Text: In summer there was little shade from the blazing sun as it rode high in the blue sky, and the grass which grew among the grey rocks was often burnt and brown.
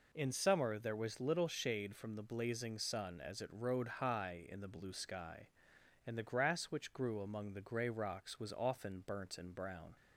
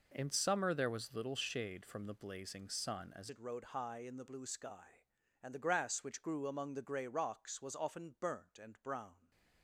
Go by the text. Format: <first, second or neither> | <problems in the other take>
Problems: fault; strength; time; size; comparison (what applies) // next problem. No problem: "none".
first | changes voice at "it"; from 3.2 s on; 6.1 s long